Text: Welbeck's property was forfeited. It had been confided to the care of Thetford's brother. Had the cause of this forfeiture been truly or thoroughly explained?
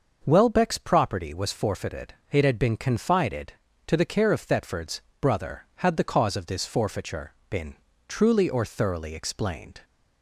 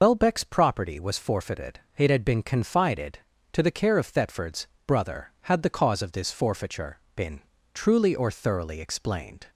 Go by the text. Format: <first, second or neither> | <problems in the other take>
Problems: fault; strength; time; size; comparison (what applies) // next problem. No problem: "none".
first | loses the start of "Welbeck's"; at 0.0 s; 125 ms // pauses between "Thetford's" and "brother"; slight; at 4.6 s; 0.20 s long; slight in the first // pauses between "forfeiture" and "been"; slight; at 6.9 s; 0.18 s long; slight in the first // pauses between "been" and "truly"; slight; at 7.3 s; 0.32 s long; slight in the first